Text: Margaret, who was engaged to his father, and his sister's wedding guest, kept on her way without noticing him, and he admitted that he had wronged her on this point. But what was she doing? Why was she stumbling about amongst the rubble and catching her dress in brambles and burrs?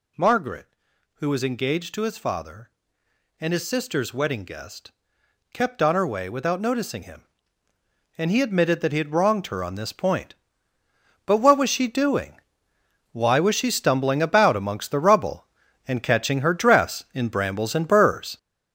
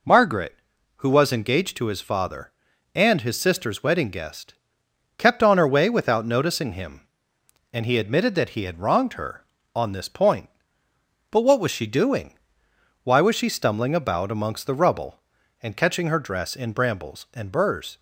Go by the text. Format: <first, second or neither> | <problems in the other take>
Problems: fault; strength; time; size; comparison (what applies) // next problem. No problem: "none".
second | gets louder; strong; throughout; 7.5 dB